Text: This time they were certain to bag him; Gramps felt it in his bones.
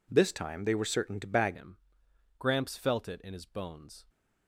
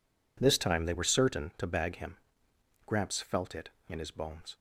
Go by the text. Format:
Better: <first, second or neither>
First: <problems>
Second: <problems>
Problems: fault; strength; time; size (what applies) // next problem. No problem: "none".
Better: second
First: changes voice at "him"; from 1.5 s on; 2.5 s long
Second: none